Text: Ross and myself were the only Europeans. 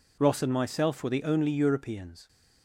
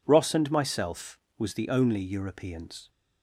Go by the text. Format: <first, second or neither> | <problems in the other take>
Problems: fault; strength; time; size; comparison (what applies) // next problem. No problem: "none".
first | says "was" for "were"; at 1.3 s